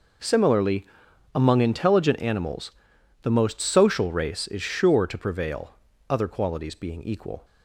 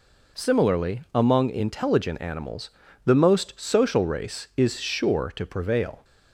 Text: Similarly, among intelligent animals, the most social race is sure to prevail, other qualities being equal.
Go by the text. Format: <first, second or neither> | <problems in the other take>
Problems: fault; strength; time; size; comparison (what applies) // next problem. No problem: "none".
first | stops before "other qualities being equal"; at 6.0 s